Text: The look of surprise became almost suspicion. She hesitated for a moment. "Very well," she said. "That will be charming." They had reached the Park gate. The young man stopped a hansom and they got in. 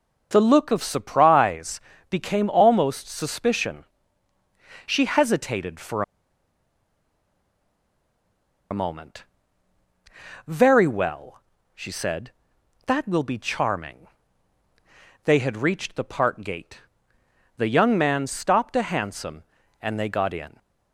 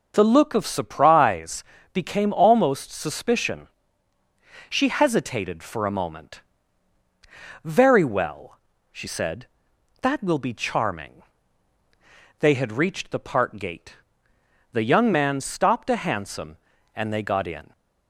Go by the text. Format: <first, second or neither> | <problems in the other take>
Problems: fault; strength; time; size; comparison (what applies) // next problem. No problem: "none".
second | pauses between "surprise" and "became"; slight; at 1.7 s; 0.30 s long; slight in the second // pauses between "for" and "a"; strong; at 6.0 s; 2.6 s long